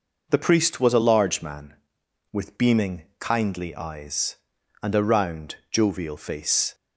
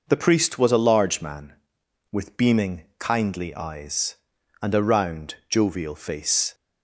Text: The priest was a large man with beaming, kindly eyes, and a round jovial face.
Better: neither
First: none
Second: none

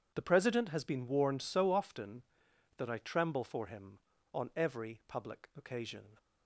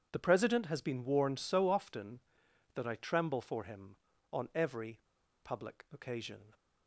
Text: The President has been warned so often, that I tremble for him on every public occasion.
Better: first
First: none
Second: pauses between "every" and "public"; at 4.9 s; 0.43 s long

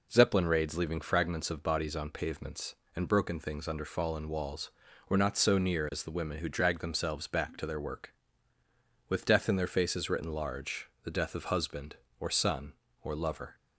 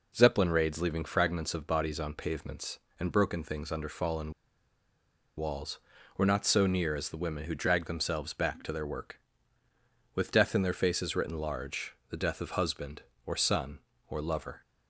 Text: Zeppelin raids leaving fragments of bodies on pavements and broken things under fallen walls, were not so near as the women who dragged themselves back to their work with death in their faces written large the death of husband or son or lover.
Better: first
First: pauses between "large" and "the"; slight; at 10.8 s; 0.16 s long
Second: pauses between "fallen" and "walls"; at 4.3 s; 1.0 s long // pauses between "large" and "the"; slight; at 11.9 s; 0.16 s long

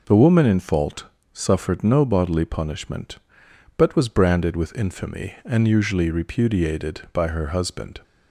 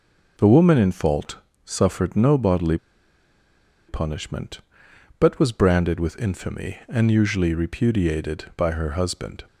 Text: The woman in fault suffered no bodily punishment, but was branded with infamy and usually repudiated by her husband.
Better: first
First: pauses between "fault" and "suffered"; slight; at 1.0 s; 0.28 s long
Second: pauses between "fault" and "suffered"; slight; at 1.3 s; 0.28 s long // pauses between "bodily" and "punishment"; at 2.7 s; 1.1 s long

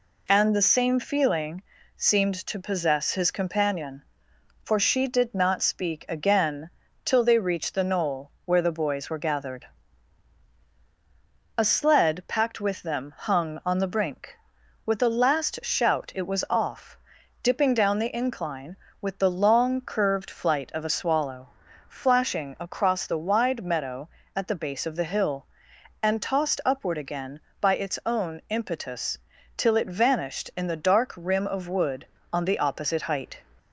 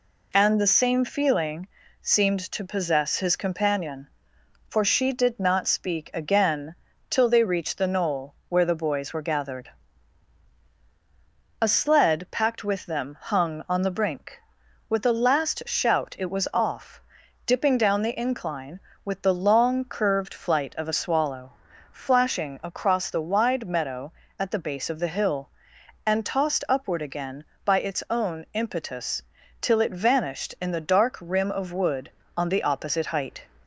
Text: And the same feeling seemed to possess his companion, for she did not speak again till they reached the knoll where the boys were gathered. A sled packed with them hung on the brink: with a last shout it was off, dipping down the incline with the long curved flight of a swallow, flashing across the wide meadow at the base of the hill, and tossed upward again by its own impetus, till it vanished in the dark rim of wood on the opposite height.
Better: neither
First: pauses between "feeling" and "seemed"; slight; at 1.6 s; 0.32 s long // pauses between "again" and "till"; slight; at 6.6 s; 0.36 s long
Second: pauses between "feeling" and "seemed"; slight; at 1.6 s; 0.32 s long // pauses between "again" and "till"; slight; at 6.7 s; 0.36 s long

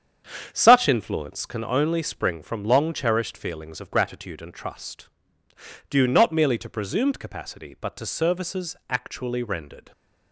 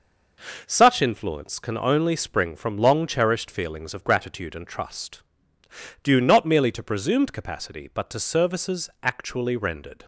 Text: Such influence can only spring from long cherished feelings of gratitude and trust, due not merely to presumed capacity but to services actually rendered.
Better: second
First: starts louder than the rest; strong; until 1.6 s; 8 dB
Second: none

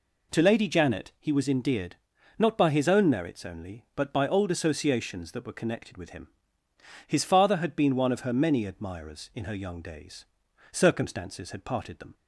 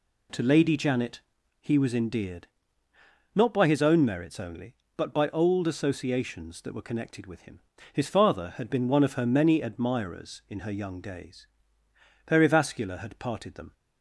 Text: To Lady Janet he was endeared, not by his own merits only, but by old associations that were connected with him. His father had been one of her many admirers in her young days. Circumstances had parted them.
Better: first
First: none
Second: pauses between "Janet" and "he"; at 1.1 s; 0.40 s long // says "Perivascular" for "Circumstances"; at 12.2 s

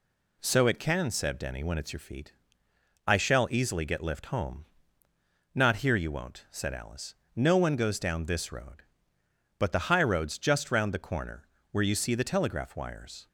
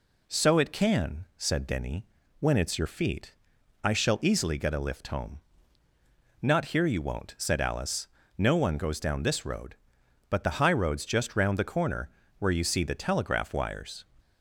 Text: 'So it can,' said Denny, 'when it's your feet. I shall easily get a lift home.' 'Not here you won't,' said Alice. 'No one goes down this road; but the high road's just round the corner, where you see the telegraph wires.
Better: second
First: skips "a"; at 4.0 s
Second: none

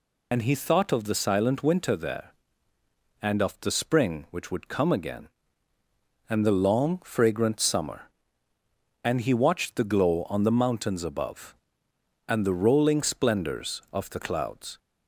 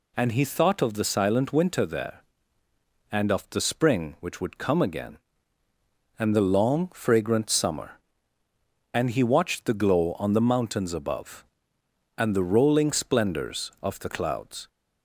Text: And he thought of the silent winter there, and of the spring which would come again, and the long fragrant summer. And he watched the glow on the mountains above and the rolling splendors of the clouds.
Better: second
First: loses the start of "And"; at 0.3 s; 55 ms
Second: none

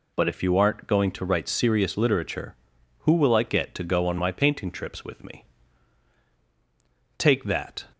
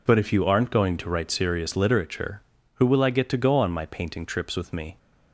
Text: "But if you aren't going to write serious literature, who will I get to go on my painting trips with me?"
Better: second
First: goes on to say "Take that"; noticeable; from 7.1 s on; 0.70 s long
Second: none

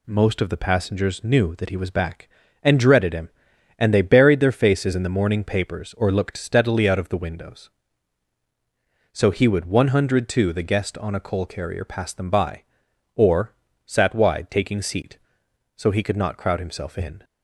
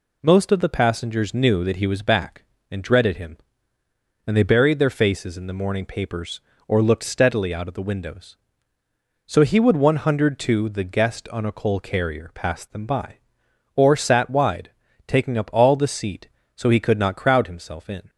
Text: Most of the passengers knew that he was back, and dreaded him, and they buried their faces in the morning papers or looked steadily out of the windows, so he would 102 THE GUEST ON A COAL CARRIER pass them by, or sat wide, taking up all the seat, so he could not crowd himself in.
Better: second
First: pauses between "or" and "sat"; slight; at 13.5 s; 0.32 s long // skips "up all the"; at 14.8 s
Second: none

